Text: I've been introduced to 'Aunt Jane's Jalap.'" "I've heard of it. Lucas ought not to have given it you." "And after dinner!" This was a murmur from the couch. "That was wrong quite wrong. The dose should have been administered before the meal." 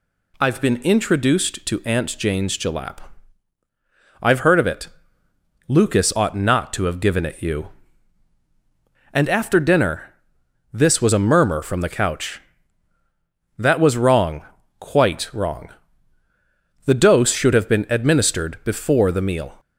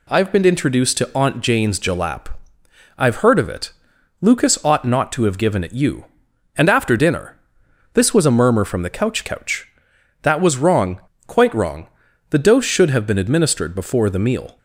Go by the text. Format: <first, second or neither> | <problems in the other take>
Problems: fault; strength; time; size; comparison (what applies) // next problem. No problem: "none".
first | says "couch" twice; at 9.2 s // pauses between "wrong" and "quite"; slight; at 11.0 s; 0.26 s long; slight in the first